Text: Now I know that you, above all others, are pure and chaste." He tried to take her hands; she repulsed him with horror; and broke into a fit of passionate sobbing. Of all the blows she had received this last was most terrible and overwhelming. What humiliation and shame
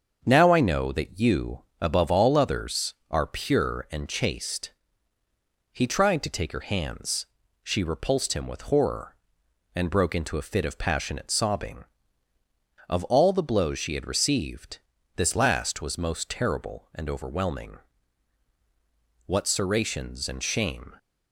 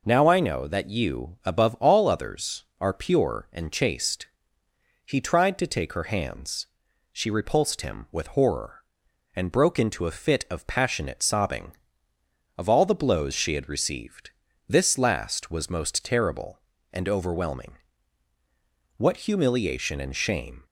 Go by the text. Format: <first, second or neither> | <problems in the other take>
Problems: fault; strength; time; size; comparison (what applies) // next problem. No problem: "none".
second | starts louder than the rest; until 1.2 s; 7 dB // pauses between "received" and "this"; at 14.7 s; 0.38 s long; slight in the second // says "serrations" for "humiliation"; at 19.4 s